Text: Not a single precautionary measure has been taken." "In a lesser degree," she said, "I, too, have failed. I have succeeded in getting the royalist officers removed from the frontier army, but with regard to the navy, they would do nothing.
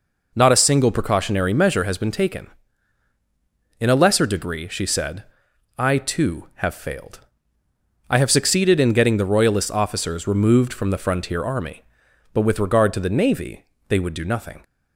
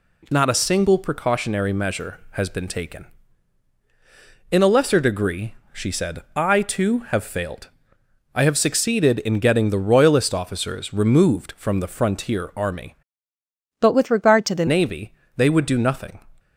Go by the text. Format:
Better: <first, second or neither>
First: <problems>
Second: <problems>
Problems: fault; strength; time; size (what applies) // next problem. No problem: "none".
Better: first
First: none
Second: changes voice from "but" to "the"; from 13.7 to 14.6 s; 0.9 s long